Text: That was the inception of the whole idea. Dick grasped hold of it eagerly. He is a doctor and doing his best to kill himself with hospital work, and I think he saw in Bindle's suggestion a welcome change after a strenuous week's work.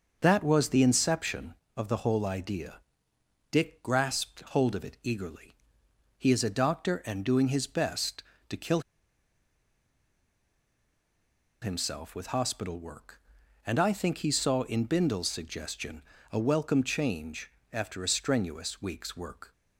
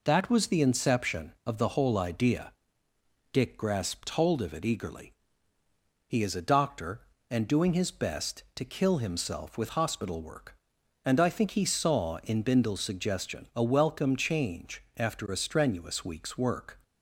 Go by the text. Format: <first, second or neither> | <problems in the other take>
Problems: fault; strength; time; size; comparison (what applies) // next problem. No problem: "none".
second | starts louder than the rest; until 1.2 s; 6.5 dB // pauses between "kill" and "himself"; strong; at 8.8 s; 2.8 s long // pauses between "suggestion" and "a"; slight; at 16.0 s; 0.30 s long // pauses between "change" and "after"; slight; at 17.4 s; 0.20 s long; slight in the second